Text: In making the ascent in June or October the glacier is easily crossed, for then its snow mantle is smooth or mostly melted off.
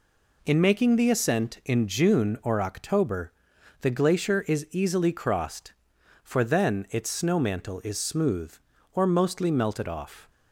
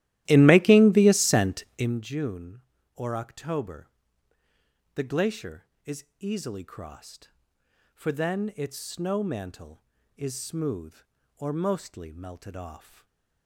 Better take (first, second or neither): first